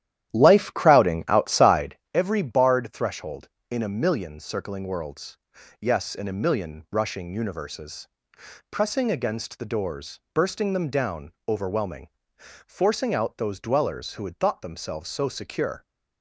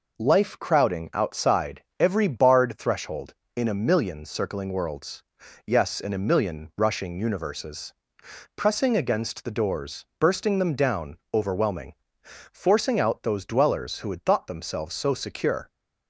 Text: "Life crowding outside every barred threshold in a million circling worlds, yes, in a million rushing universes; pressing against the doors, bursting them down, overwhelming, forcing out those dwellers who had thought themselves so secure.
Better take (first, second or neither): second